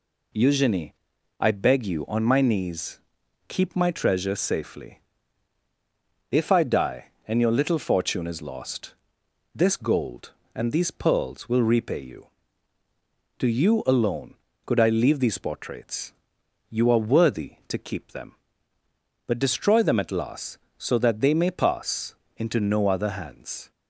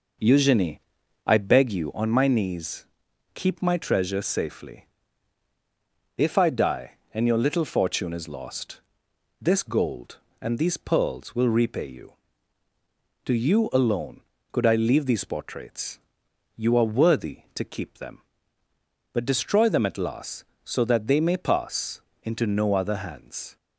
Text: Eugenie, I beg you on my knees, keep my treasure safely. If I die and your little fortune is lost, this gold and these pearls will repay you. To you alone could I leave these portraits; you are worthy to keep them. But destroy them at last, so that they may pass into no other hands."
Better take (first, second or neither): first